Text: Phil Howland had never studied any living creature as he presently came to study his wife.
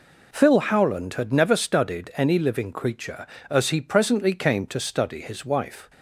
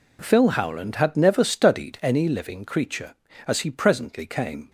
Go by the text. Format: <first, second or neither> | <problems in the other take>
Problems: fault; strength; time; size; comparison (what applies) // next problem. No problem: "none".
first | stops before "to study his wife"; at 4.6 s